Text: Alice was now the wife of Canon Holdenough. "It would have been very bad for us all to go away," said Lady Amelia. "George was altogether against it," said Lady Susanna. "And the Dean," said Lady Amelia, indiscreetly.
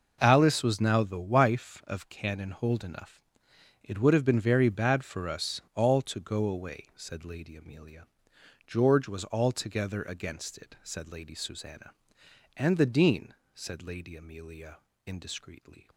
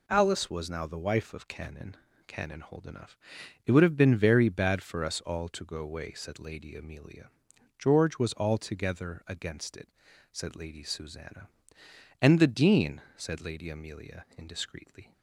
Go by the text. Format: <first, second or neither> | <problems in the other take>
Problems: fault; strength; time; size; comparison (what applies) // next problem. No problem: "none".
first | says "Canon" twice; at 2.2 s